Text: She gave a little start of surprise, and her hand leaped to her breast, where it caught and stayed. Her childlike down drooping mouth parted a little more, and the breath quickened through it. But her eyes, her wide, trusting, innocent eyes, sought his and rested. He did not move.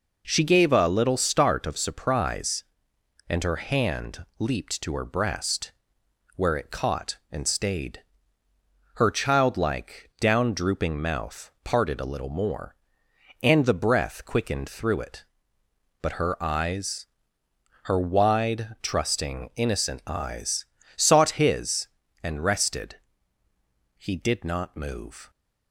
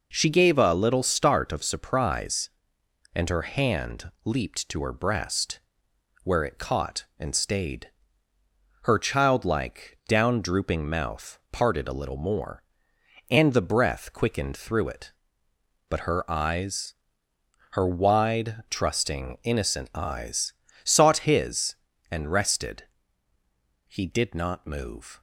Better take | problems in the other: neither | none

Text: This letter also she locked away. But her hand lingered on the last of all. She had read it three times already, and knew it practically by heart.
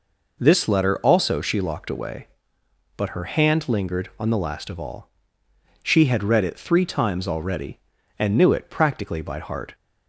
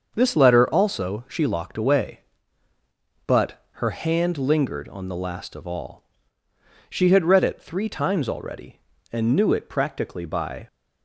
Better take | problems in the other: first | starts louder than the rest; until 1.1 s; 6.5 dB // stops before "heart"; at 10.6 s

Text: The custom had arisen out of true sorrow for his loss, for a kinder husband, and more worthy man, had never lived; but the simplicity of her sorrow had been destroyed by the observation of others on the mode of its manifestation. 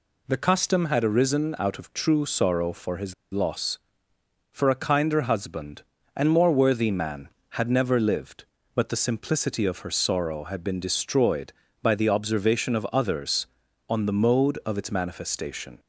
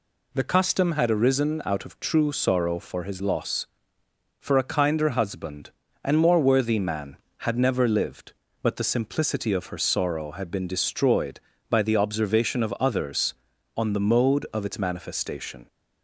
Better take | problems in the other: second | pauses between "his" and "loss"; slight; at 3.1 s; 0.18 s long

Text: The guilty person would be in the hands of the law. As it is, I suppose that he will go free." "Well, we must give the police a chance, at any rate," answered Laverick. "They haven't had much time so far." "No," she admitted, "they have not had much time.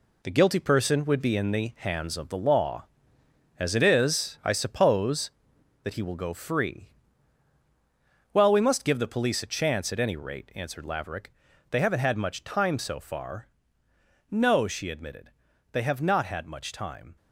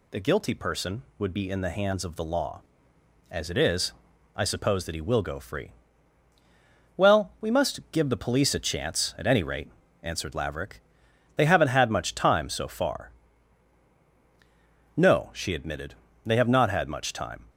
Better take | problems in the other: second | gets quieter; strong; throughout; 7.5 dB

